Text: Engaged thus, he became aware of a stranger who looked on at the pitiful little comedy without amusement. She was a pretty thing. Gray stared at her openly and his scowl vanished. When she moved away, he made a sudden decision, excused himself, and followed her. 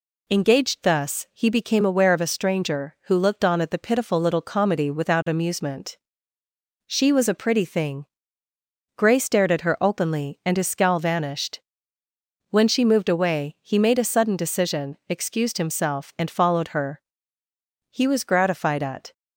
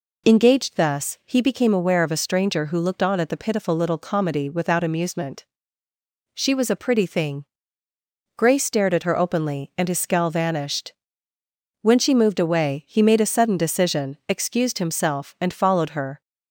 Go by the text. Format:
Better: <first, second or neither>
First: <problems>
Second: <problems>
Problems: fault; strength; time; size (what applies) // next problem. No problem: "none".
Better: second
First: goes on to say "He was gratified at"; noticeable; from 17.8 s on; 1.2 s long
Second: none